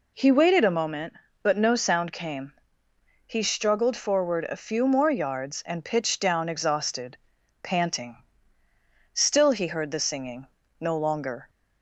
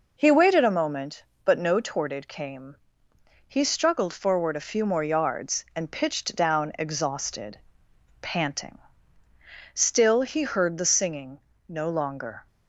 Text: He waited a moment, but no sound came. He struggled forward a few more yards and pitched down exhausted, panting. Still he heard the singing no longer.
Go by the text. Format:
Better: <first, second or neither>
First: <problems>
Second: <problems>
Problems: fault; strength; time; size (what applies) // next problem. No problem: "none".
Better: first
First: pauses between "singing" and "no"; slight; at 10.4 s; 0.34 s long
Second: says "torted" for "sound"; at 1.7 s // pauses between "singing" and "no"; slight; at 11.3 s; 0.30 s long